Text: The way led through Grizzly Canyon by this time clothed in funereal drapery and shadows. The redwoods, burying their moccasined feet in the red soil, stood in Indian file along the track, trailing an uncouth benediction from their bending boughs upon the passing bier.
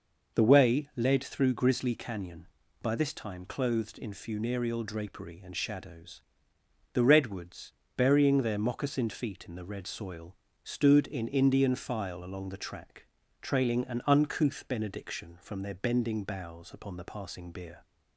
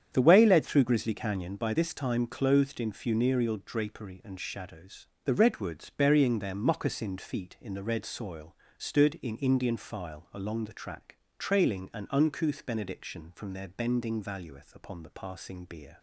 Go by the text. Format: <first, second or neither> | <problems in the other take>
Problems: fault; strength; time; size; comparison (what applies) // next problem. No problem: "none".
first | starts louder than the rest; strong; until 1.1 s; 8.5 dB // says "valueth" for "boughs"; at 14.2 s